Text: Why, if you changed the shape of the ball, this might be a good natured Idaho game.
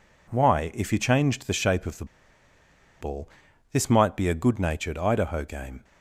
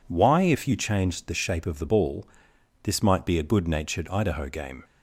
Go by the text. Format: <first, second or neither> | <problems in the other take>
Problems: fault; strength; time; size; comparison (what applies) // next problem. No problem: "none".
second | pauses between "the" and "ball"; noticeable; at 2.0 s; 0.96 s long